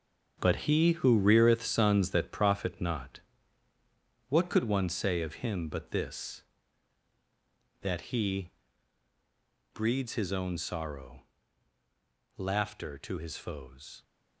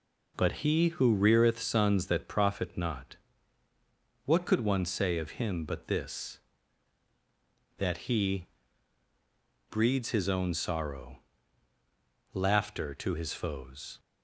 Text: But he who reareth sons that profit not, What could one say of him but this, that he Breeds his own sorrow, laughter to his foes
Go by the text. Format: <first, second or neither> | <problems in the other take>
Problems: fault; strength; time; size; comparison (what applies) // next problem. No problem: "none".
second | gets quieter; strong; throughout; 10 dB // pauses between "he" and "Breeds"; at 8.5 s; 1.2 s long; also in the second